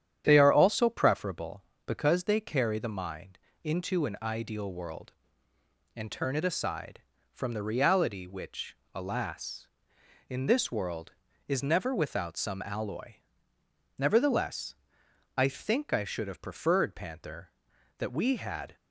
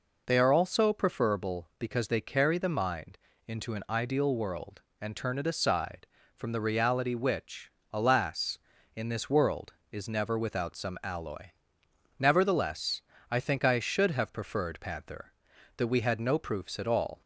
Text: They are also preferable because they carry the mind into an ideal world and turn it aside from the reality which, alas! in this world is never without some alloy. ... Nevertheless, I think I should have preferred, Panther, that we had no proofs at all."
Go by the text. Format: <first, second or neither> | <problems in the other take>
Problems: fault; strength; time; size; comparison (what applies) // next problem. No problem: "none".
second | starts louder than the rest; strong; until 1.2 s; 9.5 dB // pauses between "mind" and "into"; slight; at 3.3 s; 0.26 s long; slight in the second // stops before "no proofs at all"; at 18.7 s